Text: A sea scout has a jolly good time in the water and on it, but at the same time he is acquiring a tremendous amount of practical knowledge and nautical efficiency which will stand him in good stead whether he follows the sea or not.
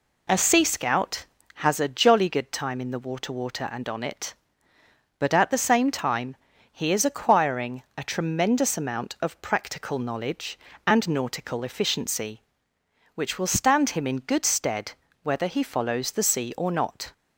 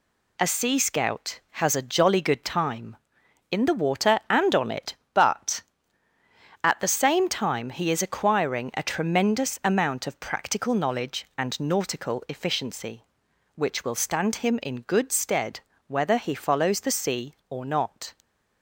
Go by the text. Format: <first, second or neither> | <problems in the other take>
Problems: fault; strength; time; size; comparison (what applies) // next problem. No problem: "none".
second | says "water" twice; at 3.3 s // pauses between "time" and "he"; at 6.3 s; 0.38 s long // pauses between "stead" and "whether"; slight; at 14.9 s; 0.32 s long; slight in the second